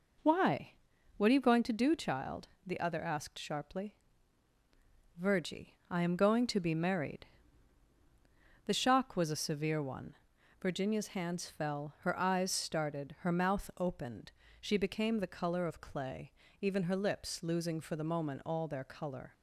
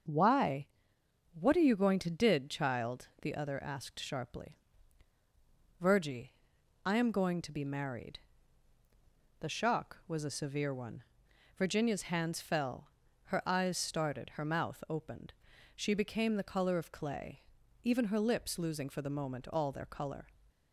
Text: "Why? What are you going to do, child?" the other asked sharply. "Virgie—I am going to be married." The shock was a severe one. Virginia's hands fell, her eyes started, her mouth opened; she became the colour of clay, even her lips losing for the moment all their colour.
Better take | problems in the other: first | starts louder than the rest; until 1.7 s; 6.5 dB // says "did" for "do"; at 2.1 s

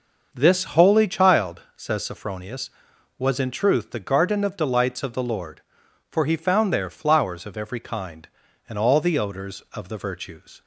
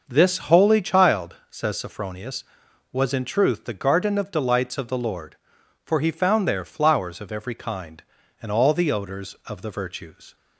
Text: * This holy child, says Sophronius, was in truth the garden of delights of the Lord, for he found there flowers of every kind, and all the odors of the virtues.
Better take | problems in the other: neither | starts louder than the rest; noticeable; the same in both

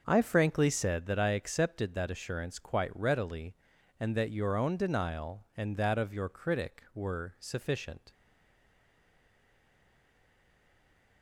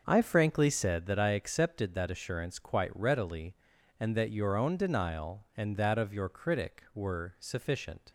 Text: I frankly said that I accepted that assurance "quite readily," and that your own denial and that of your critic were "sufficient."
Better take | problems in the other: second | starts louder than the rest; noticeable; until 1.0 s; 6 dB; noticeable in the second // stays silent after the last word; strong; from 8.1 s on; 3.1 s long

